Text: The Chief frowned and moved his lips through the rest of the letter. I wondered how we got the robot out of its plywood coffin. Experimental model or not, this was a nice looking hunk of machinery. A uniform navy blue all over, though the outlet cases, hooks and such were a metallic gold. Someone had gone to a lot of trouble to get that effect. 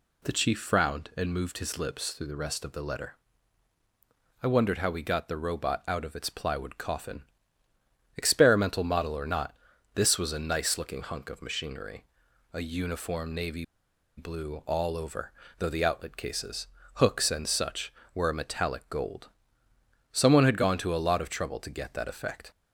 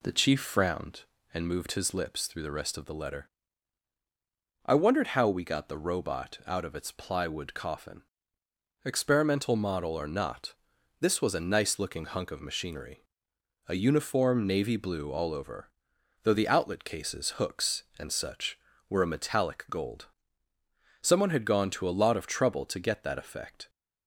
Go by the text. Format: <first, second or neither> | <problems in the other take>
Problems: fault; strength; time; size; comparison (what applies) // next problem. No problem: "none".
second | pauses between "navy" and "blue"; noticeable; at 13.6 s; 0.53 s long